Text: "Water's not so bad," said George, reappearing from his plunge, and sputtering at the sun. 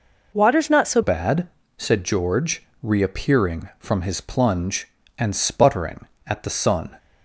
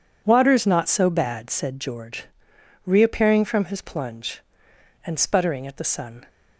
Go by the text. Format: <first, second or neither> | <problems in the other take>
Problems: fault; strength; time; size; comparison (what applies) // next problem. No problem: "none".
second | changes voice at "bad"; from 1.0 s on; 5.9 s long